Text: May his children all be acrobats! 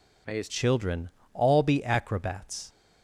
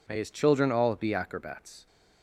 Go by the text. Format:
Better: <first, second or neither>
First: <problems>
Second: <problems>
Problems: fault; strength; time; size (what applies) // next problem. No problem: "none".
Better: second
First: changes voice at "children"; from 0.4 s on; 2.2 s long // pauses between "children" and "all"; slight; at 1.0 s; 0.24 s long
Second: none